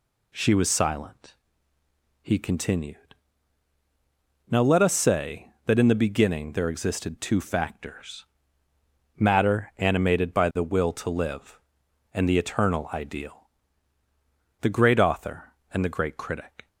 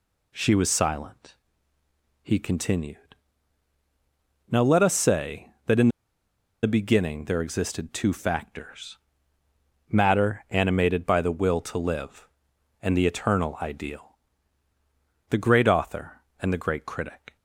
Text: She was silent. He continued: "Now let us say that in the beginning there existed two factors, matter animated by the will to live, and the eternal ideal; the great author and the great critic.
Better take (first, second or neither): first